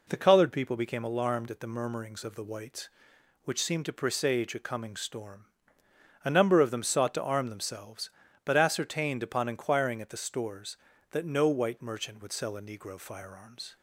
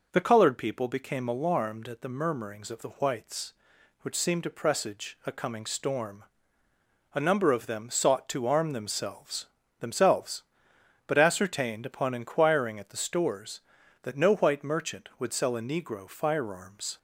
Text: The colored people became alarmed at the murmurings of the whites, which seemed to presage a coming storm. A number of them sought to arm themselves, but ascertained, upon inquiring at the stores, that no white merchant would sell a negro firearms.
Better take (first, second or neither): first